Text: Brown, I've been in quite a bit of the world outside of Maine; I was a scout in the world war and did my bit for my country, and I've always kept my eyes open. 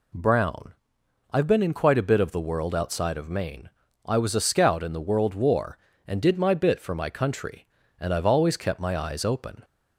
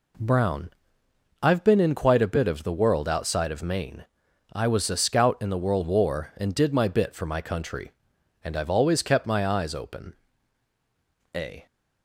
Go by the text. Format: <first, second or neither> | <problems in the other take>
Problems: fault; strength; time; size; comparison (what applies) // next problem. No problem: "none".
first | goes on to say "A"; slight; from 11.3 s on; 0.32 s long